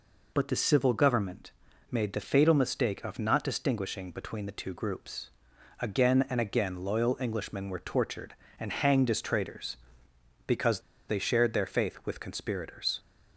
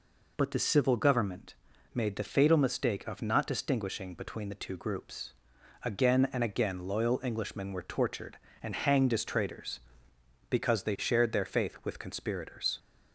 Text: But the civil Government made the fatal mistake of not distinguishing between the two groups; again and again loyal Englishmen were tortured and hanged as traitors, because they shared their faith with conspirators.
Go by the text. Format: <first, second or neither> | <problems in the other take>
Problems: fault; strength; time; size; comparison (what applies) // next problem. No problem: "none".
second | pauses between "Government" and "made"; at 1.5 s; 0.40 s long; also in the second // pauses between "because" and "they"; slight; at 10.8 s; 0.27 s long